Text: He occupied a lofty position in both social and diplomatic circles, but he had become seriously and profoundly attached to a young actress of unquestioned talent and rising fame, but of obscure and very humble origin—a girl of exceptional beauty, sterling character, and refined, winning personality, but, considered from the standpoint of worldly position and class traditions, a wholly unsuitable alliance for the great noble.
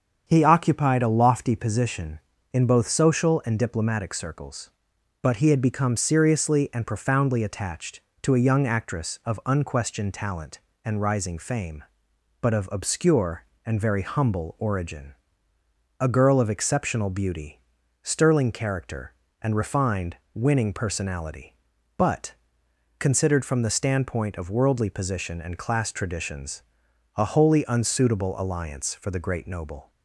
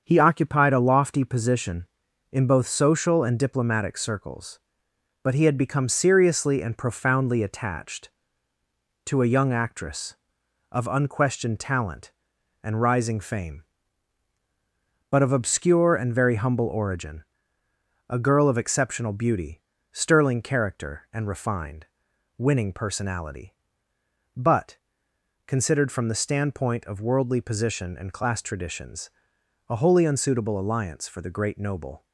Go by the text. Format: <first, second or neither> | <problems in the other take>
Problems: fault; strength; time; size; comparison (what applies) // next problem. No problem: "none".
neither | starts louder than the rest; the same in both